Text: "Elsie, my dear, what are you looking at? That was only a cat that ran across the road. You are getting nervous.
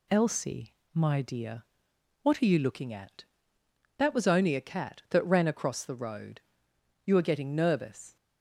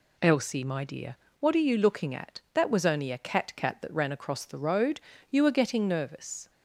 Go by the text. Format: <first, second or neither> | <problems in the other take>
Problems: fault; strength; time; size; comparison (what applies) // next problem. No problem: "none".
first | says "cat" twice; at 3.5 s